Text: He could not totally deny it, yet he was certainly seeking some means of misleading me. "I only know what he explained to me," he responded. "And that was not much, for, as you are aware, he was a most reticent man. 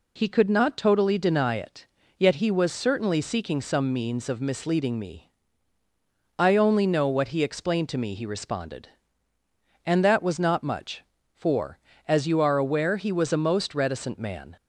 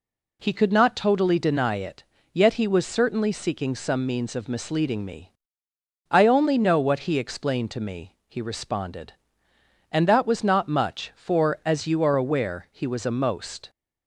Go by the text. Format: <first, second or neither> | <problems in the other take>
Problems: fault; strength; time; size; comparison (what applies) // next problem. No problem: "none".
first | stops before "reticent man"; at 13.6 s